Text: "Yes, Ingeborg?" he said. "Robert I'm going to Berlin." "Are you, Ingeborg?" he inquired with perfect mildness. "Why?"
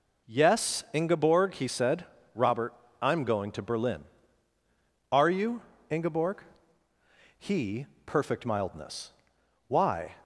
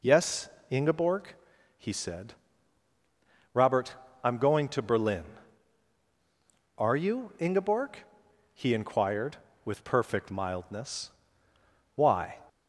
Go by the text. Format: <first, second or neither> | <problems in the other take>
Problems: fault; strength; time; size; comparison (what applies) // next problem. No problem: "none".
second | pauses between "Robert" and "I'm"; slight; at 2.7 s; 0.30 s long; slight in the second // skips "inquired with"; at 7.9 s